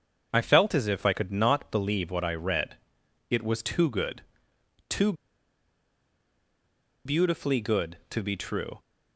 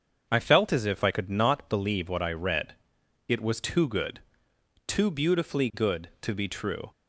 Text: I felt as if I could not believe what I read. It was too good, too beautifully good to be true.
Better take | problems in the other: second | starts louder than the rest; until 1.3 s; 7 dB; also in the second // pauses between "too" and "beautifully"; strong; at 5.1 s; 1.9 s long

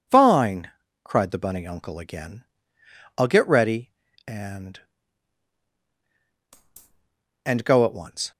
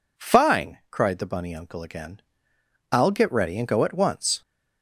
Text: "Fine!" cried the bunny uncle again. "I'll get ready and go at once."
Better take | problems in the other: second | says "and" twice; at 7.4 s

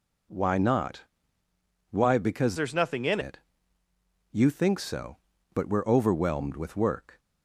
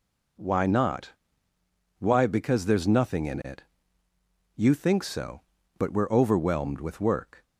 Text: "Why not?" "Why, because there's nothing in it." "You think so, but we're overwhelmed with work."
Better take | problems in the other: second | changes voice from "there's" to "in"; from 2.5 to 3.1 s; 0.6 s long

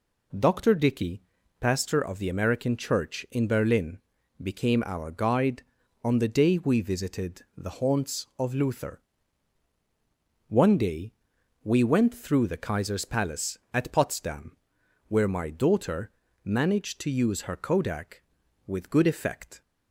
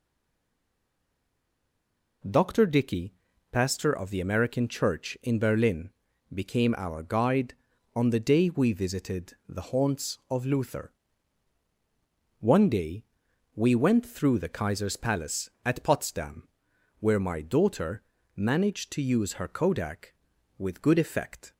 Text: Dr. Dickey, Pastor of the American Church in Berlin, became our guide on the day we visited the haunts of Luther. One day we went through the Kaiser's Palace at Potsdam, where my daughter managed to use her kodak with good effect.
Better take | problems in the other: first | stays silent before the first word; until 2.2 s; 2.2 s long // pauses between "visited" and "the"; slight; at 9.3 s; 0.16 s long; slight in the first // pauses between "day" and "we"; noticeable; at 13.0 s; 0.50 s long; noticeable in the first // pauses between "daughter" and "managed"; slight; at 18.0 s; 0.34 s long; slight in the first

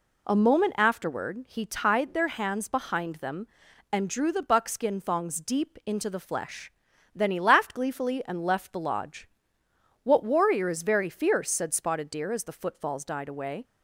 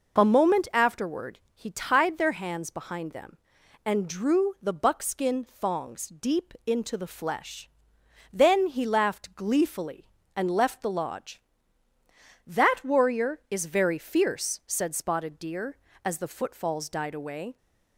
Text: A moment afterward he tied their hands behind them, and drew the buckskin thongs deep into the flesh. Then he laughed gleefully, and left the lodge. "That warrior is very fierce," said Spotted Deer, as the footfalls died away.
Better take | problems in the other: second | says "What" for "That"; at 10.0 s

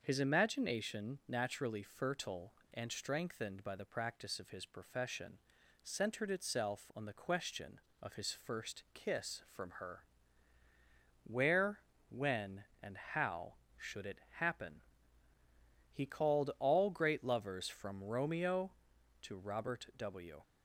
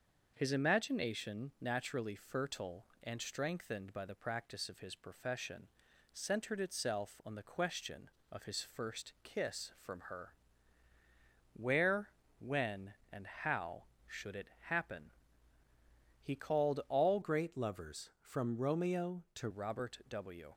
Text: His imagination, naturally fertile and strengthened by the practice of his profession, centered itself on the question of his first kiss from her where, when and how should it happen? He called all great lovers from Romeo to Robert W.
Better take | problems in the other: first | starts louder than the rest; until 1.3 s; 6.5 dB; also in the first // pauses between "her" and "where"; at 10.3 s; 1.2 s long; also in the first // pauses between "it" and "happen"; slight; at 14.4 s; 0.22 s long; slight in the first // changes voice from "great" to "to"; from 17.2 to 19.4 s; 2.2 s long

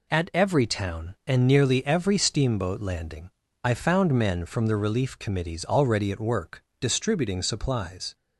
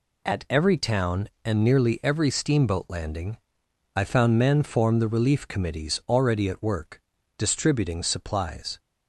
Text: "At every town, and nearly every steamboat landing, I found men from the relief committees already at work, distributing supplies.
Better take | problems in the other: first | says "form" for "from"; at 4.6 s

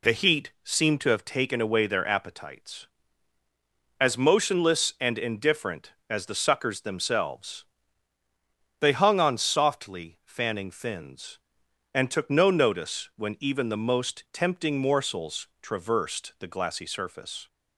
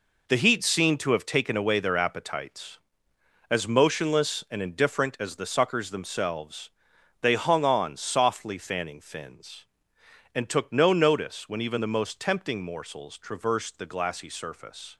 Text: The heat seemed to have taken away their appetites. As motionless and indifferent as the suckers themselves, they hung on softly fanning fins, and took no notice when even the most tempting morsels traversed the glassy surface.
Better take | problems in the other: first | gets quieter; strong; throughout; 8.5 dB

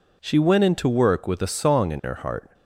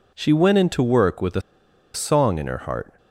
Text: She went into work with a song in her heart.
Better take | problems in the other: first | pauses between "a" and "song"; noticeable; at 1.3 s; 0.54 s long

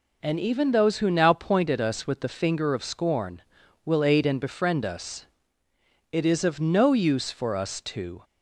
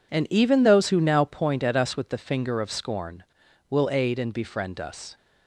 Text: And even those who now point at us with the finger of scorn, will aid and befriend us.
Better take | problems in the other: second | goes on to say "It is of no use for us to"; strong; from 6.1 s on; 2.1 s long

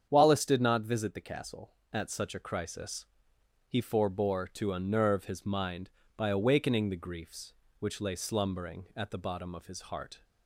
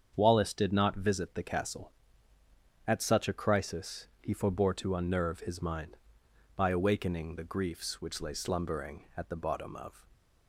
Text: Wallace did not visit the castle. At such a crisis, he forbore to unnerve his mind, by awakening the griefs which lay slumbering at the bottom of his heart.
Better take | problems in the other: first | starts louder than the rest; strong; until 1.1 s; 7.5 dB; strong in the first // stops before "his heart"; at 10.1 s

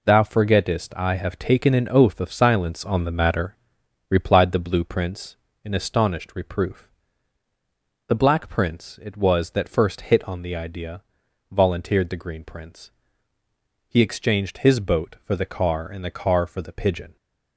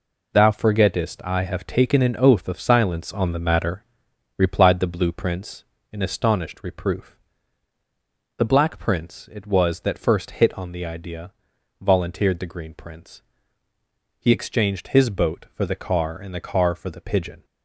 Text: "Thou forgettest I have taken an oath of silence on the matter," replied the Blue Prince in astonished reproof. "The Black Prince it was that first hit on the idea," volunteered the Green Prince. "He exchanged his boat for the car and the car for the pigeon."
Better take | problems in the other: neither | none

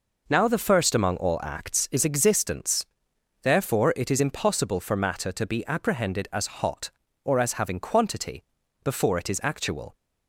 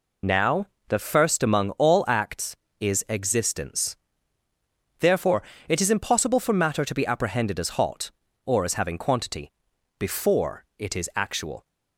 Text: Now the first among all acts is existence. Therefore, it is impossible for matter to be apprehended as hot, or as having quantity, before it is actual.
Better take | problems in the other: first | loses the start of "Now"; at 0.2 s; 50 ms // pauses between "Now" and "the"; slight; at 0.6 s; 0.21 s long // pauses between "before" and "it"; slight; at 10.6 s; 0.16 s long

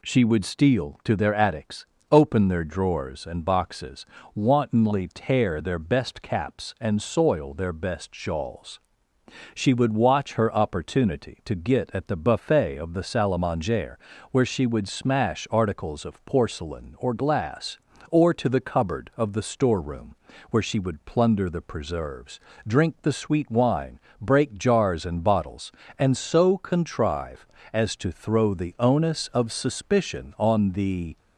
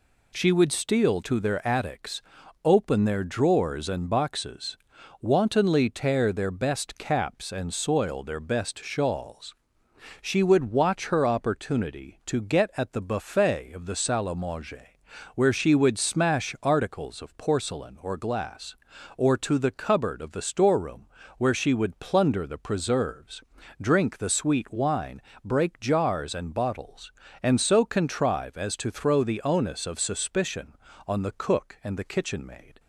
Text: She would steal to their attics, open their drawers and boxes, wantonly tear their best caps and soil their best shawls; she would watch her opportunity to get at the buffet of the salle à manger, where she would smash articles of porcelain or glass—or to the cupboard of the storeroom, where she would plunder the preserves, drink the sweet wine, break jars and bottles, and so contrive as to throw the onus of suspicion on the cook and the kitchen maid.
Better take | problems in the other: second | stops before "cook and the kitchen maid"; at 31.1 s

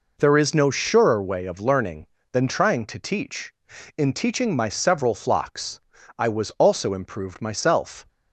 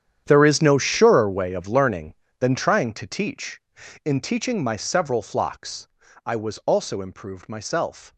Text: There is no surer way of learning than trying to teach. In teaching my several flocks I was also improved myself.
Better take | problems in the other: first | gets quieter; strong; throughout; 16.5 dB // pauses between "flocks" and "I"; slight; at 5.8 s; 0.36 s long; slight in the first

